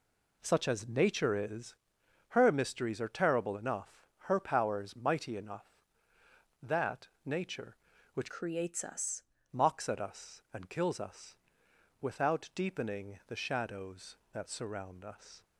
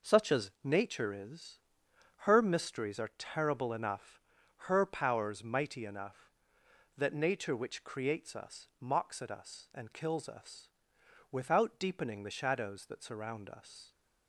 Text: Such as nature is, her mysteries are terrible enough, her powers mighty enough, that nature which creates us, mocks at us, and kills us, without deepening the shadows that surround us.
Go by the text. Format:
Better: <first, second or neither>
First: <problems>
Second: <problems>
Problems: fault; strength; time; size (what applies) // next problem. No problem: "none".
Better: second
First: pauses between "that" and "nature"; slight; at 7.0 s; 0.18 s long // changes voice from "creates" to "us"; from 8.2 to 9.2 s; 1.0 s long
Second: none